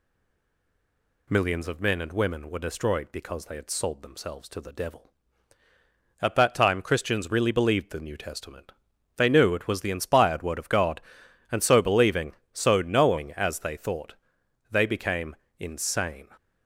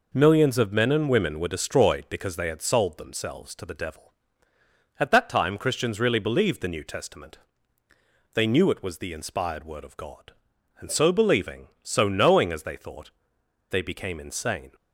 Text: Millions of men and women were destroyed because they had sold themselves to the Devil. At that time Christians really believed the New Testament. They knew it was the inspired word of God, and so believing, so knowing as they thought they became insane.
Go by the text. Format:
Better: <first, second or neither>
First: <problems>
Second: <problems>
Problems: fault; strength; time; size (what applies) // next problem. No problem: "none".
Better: second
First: stays silent before the first word; noticeable; until 1.2 s; 1.2 s long // pauses between "thought" and "they"; noticeable; at 14.1 s; 0.56 s long // pauses between "became" and "insane"; slight; at 15.3 s; 0.24 s long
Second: pauses between "thought" and "they"; noticeable; at 13.0 s; 0.60 s long